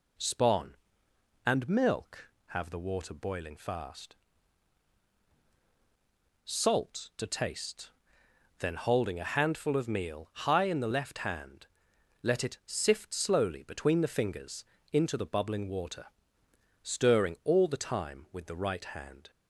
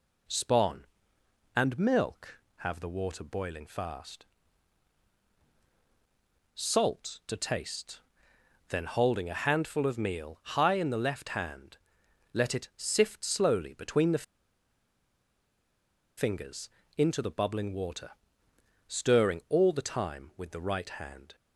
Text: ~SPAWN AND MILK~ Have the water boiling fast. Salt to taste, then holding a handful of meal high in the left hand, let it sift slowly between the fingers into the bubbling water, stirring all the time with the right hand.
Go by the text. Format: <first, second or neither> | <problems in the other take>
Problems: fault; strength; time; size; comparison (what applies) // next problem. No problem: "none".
first | pauses between "the" and "fingers"; strong; at 14.2 s; 1.9 s long // pauses between "fingers" and "into"; slight; at 16.6 s; 0.28 s long; slight in the first